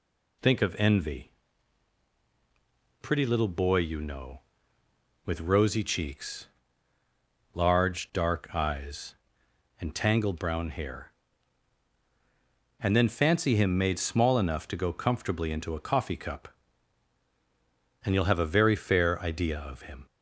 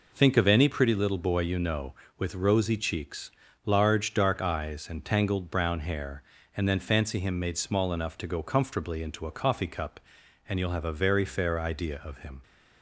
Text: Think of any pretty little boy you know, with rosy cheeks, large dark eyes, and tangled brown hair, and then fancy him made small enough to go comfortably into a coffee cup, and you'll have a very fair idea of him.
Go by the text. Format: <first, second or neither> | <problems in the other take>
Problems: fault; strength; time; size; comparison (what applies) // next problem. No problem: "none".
second | says "envy" for "any"; at 0.7 s